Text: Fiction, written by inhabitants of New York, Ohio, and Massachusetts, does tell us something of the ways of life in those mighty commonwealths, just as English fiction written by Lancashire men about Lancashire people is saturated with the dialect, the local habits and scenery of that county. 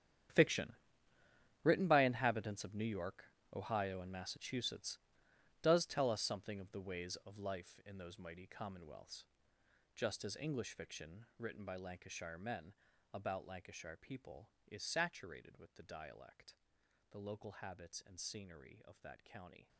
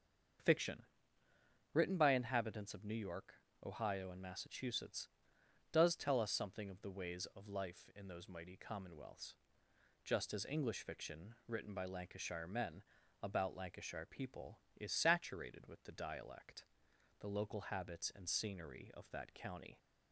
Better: second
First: gets quieter; strong; throughout; 15.5 dB // starts louder than the rest; strong; until 2.1 s; 9.5 dB // pauses between "men" and "about"; at 12.7 s; 0.40 s long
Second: starts louder than the rest; until 2.2 s; 6.5 dB // pauses between "men" and "about"; at 12.8 s; 0.40 s long

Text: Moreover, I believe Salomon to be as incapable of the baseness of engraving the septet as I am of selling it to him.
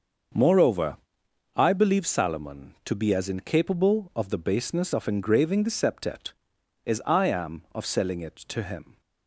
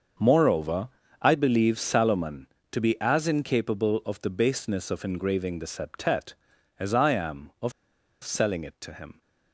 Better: first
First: starts louder than the rest; until 1.9 s; 6.5 dB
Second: starts louder than the rest; until 1.5 s; 6.5 dB // pauses between "of" and "selling"; noticeable; at 7.7 s; 0.50 s long

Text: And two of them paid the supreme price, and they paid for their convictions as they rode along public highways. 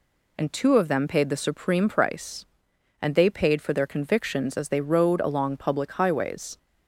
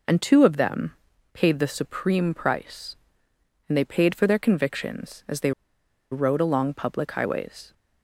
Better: first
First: none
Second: pauses between "them" and "paid"; at 0.9 s; 0.40 s long // pauses between "they" and "rode"; noticeable; at 5.5 s; 0.60 s long

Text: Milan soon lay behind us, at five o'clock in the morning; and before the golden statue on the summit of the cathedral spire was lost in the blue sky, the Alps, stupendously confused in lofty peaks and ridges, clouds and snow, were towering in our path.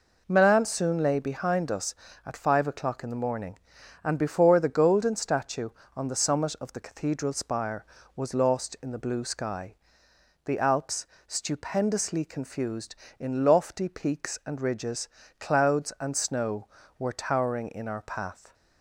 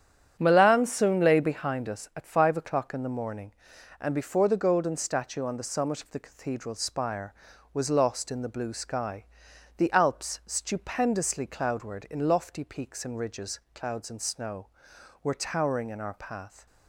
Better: first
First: none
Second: starts louder than the rest; strong; until 1.4 s; 9.5 dB // says "cloudward" for "confused"; at 11.4 s

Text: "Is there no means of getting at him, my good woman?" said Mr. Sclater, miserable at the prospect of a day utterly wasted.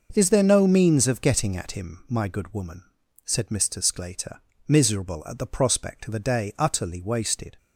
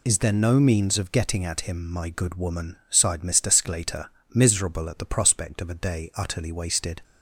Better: first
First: none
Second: says "sighed" for "said"; at 2.8 s

